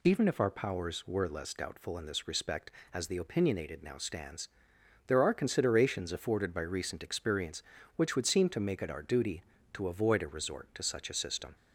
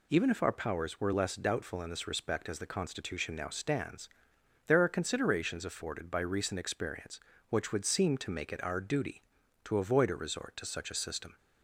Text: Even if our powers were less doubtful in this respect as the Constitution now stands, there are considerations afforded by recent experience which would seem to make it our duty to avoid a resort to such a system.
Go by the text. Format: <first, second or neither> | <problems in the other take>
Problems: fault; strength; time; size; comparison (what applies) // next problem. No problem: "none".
second | says "Opinionated" for "Constitution"; at 3.1 s